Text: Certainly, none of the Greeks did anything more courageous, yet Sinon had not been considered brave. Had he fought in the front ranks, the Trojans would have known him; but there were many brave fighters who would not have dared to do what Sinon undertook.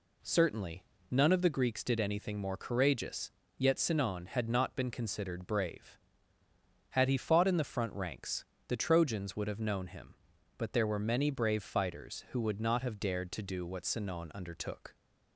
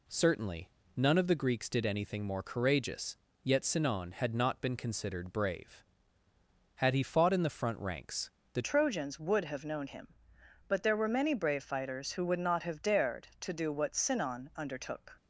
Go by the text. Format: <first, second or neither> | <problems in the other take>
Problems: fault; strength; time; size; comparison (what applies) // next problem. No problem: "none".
first | changes voice at "Trojans"; from 8.6 s on; 6.5 s long